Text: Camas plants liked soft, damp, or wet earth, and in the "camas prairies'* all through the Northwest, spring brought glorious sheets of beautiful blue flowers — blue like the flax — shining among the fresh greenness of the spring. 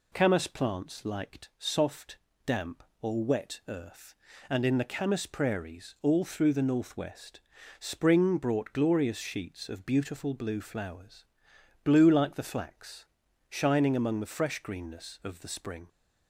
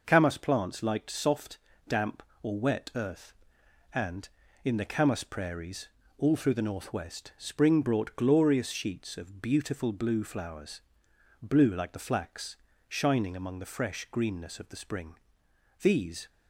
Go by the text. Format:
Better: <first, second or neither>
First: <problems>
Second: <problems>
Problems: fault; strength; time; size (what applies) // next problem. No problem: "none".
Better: first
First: none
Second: pauses between "prairies" and "all"; slight; at 5.8 s; 0.32 s long // goes on to say "These"; slight; from 15.8 s on; 0.48 s long